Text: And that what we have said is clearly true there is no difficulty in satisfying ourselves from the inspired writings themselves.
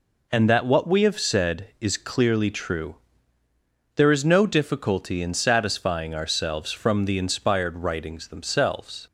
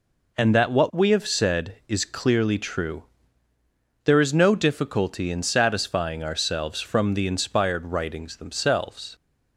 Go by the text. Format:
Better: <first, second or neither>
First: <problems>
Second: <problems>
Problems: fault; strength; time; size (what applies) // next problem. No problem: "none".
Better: neither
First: pauses between "true" and "there"; at 2.9 s; 0.98 s long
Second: pauses between "true" and "there"; at 3.0 s; 1.0 s long